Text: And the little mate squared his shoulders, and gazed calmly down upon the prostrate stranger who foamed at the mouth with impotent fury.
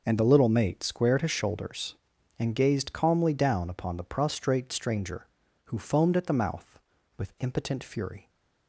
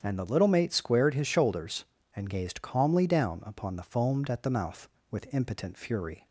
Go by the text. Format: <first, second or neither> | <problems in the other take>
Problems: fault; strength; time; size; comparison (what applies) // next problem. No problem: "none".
first | starts louder than the rest; strong; until 1.0 s; 8.5 dB // skips "prostrate stranger who"; at 3.8 s